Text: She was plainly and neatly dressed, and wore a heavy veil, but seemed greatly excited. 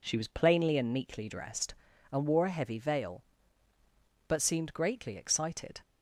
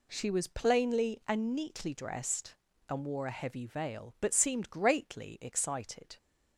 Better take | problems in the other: neither | none

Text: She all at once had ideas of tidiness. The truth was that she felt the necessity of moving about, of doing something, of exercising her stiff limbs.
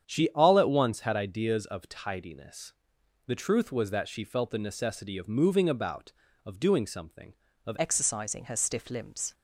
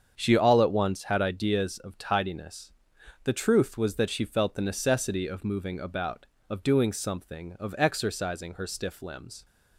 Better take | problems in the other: second | starts louder than the rest; strong; until 1.0 s; 8.5 dB; strong in the second // changes voice at "exercising"; from 7.7 s on; 1.6 s long

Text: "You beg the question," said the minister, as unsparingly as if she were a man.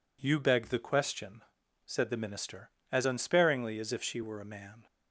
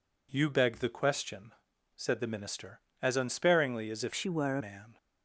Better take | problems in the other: first | changes voice from "she" to "a"; from 4.1 to 4.6 s; 0.5 s long

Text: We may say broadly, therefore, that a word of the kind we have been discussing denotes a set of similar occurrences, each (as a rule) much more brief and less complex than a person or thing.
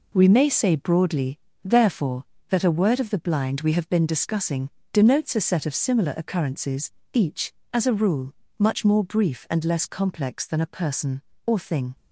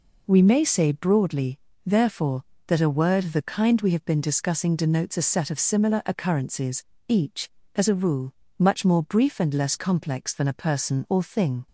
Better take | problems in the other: second | says "blind" for "kind"; at 3.1 s // pauses between "discussing" and "denotes"; slight; at 4.6 s; 0.22 s long

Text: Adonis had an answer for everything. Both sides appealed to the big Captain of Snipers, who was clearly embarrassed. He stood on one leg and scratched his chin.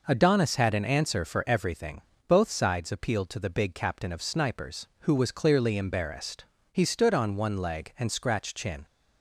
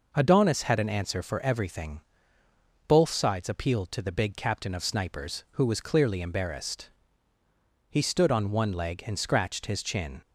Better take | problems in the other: second | skips "his"; at 8.5 s

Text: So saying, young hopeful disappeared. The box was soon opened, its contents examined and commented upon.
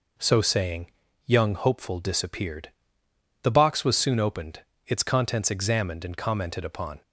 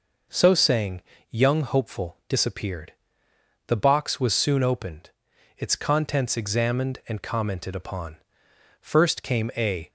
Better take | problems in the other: first | goes on to say "First came a"; noticeable; from 8.7 s on; 1.1 s long

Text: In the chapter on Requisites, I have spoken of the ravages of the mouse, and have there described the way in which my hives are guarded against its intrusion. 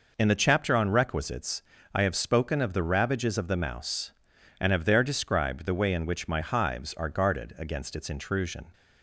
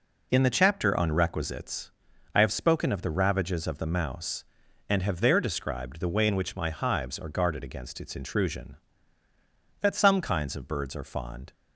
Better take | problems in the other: first | goes on to say "That some kinds of birds are fond"; strong; from 9.8 s on; 1.7 s long

